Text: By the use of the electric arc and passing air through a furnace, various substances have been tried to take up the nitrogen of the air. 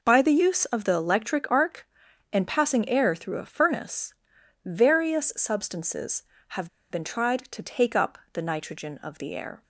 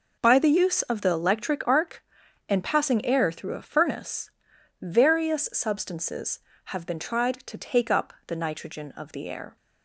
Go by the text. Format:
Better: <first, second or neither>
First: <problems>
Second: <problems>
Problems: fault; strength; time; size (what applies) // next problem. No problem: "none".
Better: second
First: pauses between "have" and "been"; slight; at 6.6 s; 0.22 s long // pauses between "up" and "the"; slight; at 8.1 s; 0.16 s long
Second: none